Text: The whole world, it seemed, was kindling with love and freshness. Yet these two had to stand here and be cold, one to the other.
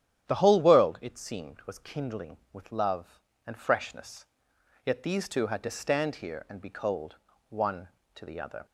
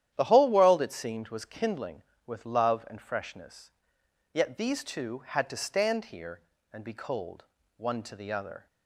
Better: neither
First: starts louder than the rest; strong; until 1.3 s; 10.5 dB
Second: starts louder than the rest; strong; until 1.1 s; 11 dB

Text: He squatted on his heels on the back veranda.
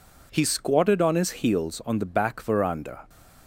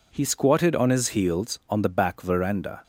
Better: neither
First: none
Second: none

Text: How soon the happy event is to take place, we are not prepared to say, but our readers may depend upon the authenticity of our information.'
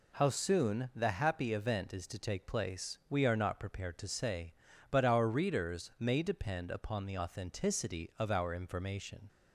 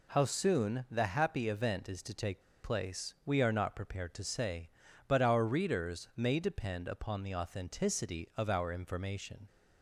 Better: first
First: none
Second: pauses between "take" and "place"; slight; at 2.4 s; 0.22 s long

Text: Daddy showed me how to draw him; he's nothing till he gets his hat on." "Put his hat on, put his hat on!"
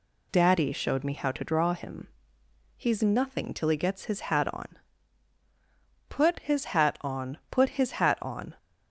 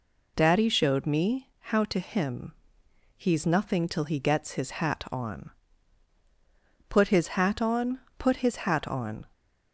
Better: first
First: none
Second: skips "draw"; at 1.9 s

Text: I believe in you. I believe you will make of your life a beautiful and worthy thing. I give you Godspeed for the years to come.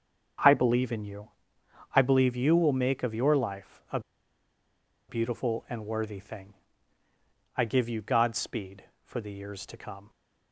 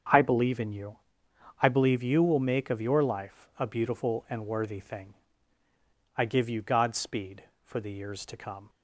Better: second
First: starts louder than the rest; strong; until 2.0 s; 7.5 dB // pauses between "a" and "beautiful"; at 3.9 s; 1.0 s long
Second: starts louder than the rest; strong; until 1.7 s; 7.5 dB

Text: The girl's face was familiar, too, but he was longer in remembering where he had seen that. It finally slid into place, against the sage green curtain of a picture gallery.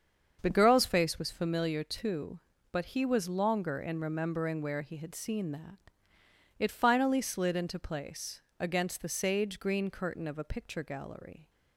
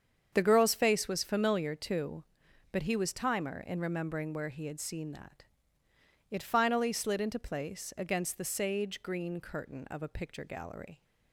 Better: first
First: starts louder than the rest; until 1.4 s; 7 dB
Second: starts louder than the rest; strong; until 1.3 s; 7.5 dB // says "timer" for "longer"; at 3.1 s

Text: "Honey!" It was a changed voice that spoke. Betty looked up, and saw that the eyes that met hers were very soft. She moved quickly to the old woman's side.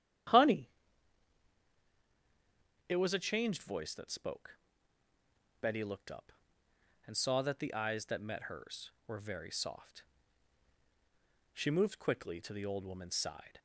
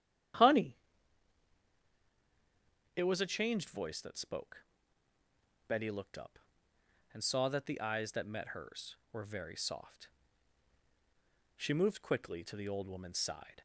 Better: neither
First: starts louder than the rest; strong; until 3.4 s; 10 dB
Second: starts louder than the rest; strong; until 3.5 s; 10 dB

